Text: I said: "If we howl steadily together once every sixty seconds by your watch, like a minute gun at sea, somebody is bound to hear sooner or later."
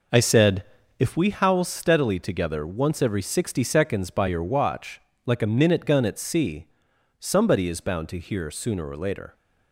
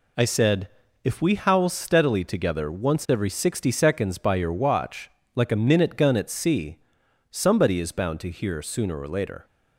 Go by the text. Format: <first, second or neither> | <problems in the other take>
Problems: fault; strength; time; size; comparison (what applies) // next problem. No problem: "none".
second | starts louder than the rest; noticeable; until 1.2 s; 5.5 dB